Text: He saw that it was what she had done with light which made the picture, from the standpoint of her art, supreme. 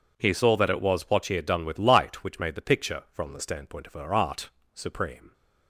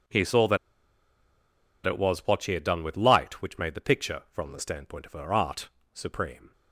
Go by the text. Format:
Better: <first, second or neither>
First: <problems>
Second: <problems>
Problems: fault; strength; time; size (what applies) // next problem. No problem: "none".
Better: first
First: none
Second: pauses between "that" and "it"; strong; at 0.5 s; 1.2 s long